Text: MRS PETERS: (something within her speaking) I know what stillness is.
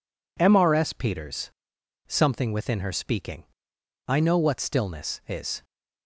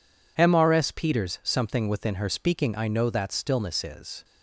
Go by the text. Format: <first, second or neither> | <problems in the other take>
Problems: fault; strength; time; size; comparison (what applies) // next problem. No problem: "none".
first | says "that" for "what"; at 3.0 s